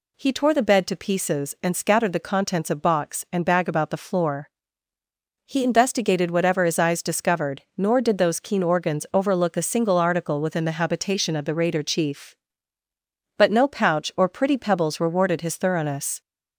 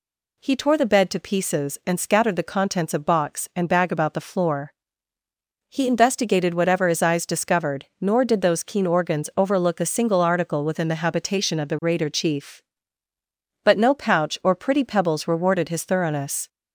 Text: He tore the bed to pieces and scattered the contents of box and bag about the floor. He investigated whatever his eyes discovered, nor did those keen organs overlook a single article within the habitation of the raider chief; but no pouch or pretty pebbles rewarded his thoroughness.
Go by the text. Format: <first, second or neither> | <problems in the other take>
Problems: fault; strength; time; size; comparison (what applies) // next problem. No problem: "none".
neither | none